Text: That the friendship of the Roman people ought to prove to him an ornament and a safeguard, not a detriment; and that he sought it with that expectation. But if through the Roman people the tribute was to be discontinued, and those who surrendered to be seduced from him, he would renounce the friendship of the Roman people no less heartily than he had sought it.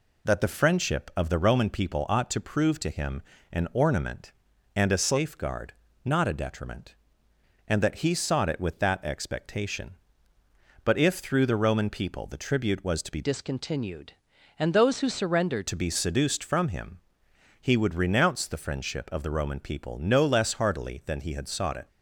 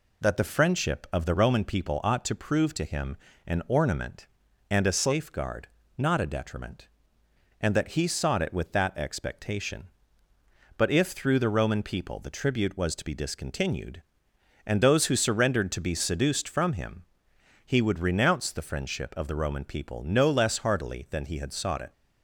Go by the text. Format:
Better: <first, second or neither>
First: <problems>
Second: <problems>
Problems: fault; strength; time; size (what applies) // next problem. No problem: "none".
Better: second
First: pauses between "him" and "an"; slight; at 3.2 s; 0.30 s long // changes voice from "discontinued" to "surrendered"; from 13.2 to 15.6 s; 2.4 s long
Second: pauses between "him" and "an"; slight; at 3.1 s; 0.30 s long